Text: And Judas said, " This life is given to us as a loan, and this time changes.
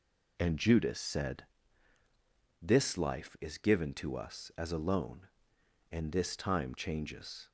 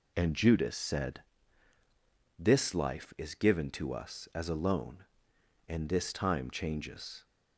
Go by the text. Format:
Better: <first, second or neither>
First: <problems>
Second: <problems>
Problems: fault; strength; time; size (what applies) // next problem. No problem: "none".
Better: neither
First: none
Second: none